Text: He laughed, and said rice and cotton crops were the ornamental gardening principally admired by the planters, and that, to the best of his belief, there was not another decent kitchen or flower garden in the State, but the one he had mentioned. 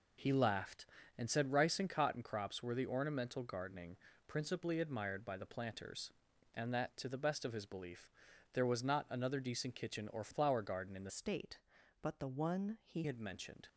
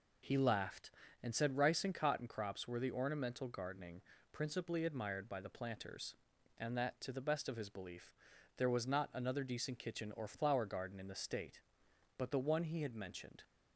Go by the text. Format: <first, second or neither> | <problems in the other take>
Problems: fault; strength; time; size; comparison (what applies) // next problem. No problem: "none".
second | pauses between "gardening" and "principally"; slight; at 3.9 s; 0.32 s long; slight in the second // changes voice from "State" to "he"; from 11.0 to 13.0 s; 2.0 s long